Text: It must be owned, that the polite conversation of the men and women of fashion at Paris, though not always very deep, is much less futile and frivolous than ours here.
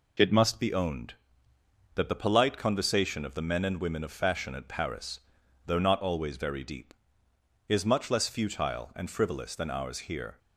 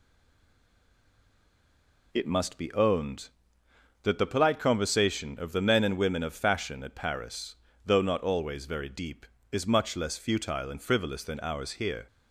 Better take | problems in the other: first | stays silent before the first word; until 2.1 s; 2.1 s long

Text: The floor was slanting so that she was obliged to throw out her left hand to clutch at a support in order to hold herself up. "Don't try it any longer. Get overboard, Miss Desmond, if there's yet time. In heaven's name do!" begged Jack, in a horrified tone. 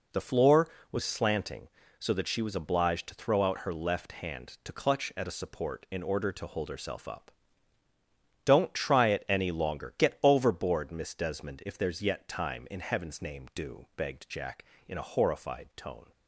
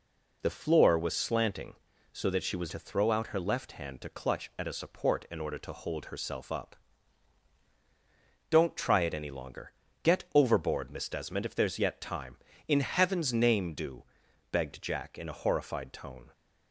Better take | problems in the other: first | skips "obliged"; at 2.7 s

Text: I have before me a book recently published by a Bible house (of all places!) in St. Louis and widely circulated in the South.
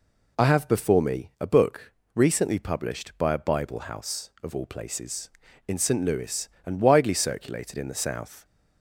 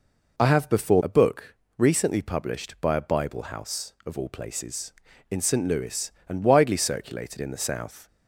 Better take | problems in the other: first | skips "me"; at 1.0 s // pauses between "book" and "recently"; slight; at 1.5 s; 0.24 s long; slight in the first

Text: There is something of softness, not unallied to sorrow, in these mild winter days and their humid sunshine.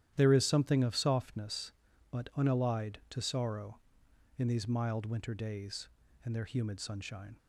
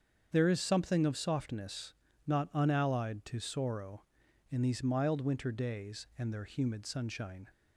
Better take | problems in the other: second | starts louder than the rest; strong; until 1.1 s; 11.5 dB; strong in the second // says "but" for "not"; at 2.1 s

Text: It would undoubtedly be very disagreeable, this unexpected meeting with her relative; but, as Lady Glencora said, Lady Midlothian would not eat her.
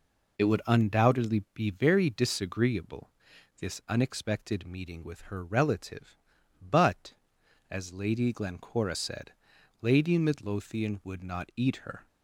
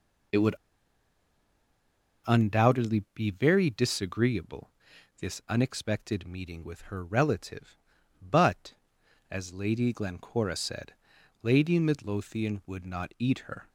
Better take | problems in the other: first | pauses between "would" and "undoubtedly"; strong; at 0.5 s; 1.7 s long

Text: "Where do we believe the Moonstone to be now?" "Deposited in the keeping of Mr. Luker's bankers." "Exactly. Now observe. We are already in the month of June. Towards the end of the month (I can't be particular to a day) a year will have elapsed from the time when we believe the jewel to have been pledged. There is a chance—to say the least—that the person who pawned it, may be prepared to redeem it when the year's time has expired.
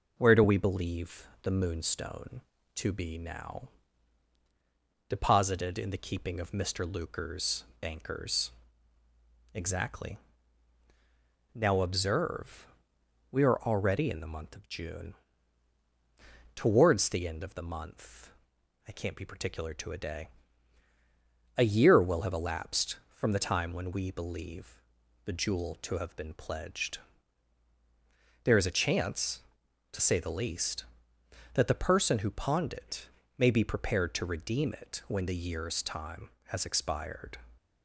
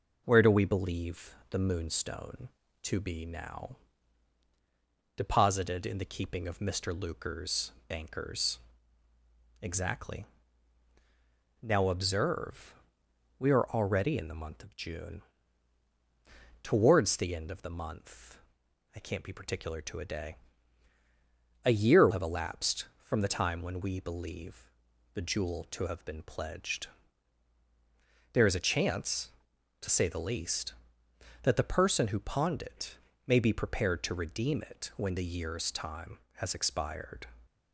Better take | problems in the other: first | pauses between "believe" and "the"; slight; at 1.3 s; 0.16 s long; slight in the first // pauses between "Luker's" and "bankers"; slight; at 7.7 s; 0.16 s long; slight in the first // skips "will"; at 22.0 s // pauses between "believe" and "the"; at 24.6 s; 0.44 s long; also in the first

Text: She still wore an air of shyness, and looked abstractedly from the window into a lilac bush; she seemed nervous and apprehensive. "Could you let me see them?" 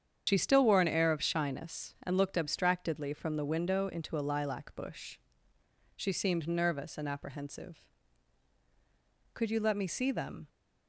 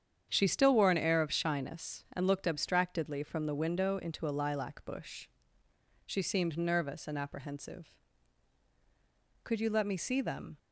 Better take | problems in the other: second | loses the start of "She"; at 0.2 s; 65 ms // starts louder than the rest; strong; until 1.2 s; 8 dB; strong in the second

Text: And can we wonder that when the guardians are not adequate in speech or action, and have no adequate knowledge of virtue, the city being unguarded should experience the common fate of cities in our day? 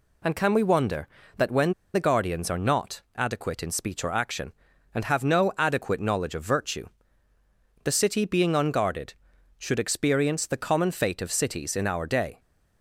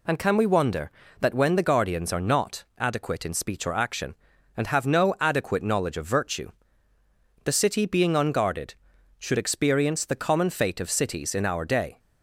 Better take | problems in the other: second | pauses between "when" and "the"; slight; at 1.7 s; 0.20 s long

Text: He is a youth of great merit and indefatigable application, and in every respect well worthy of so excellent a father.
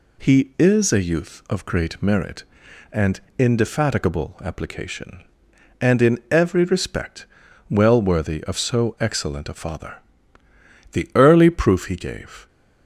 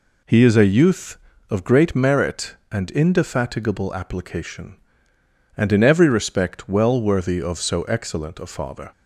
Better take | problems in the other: second | pauses between "and" and "indefatigable"; slight; at 3.2 s; 0.16 s long // pauses between "respect" and "well"; at 7.2 s; 0.44 s long // goes on to say "The early proof he gave"; from 10.9 s on; 1.5 s long

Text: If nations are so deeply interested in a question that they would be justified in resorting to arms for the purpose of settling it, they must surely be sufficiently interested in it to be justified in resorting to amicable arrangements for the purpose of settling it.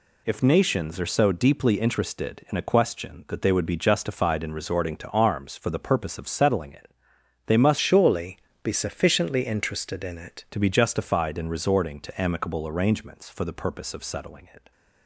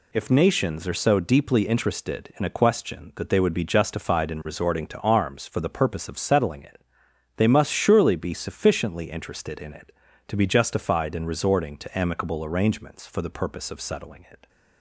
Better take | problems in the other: second | changes voice from "surely" to "it"; from 7.7 to 10.4 s; 2.7 s long // pauses between "surely" and "be"; slight; at 8.3 s; 0.24 s long

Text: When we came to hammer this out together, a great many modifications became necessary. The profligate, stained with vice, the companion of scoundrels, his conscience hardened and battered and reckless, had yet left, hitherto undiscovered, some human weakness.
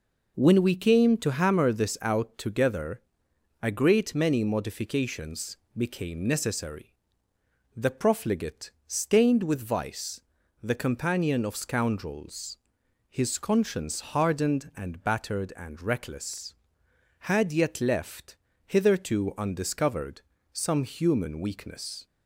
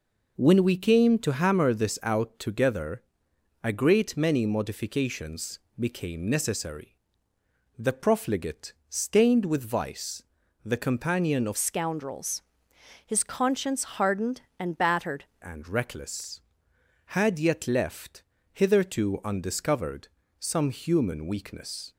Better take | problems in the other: first | pauses between "modifications" and "became"; slight; at 5.5 s; 0.20 s long; slight in the first // changes voice from "scoundrels" to "battered"; from 11.5 to 15.2 s; 3.7 s long

